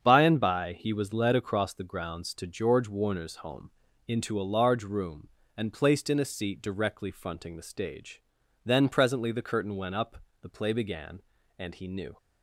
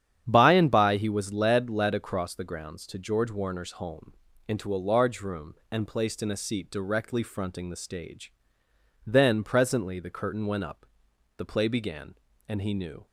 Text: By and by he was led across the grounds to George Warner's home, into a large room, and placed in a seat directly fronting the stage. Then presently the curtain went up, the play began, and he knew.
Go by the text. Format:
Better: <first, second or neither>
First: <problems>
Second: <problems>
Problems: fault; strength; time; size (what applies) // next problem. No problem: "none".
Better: first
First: starts louder than the rest; strong; until 1.0 s; 7.5 dB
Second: starts louder than the rest; strong; until 1.2 s; 9.5 dB // says "led" twice; at 1.6 s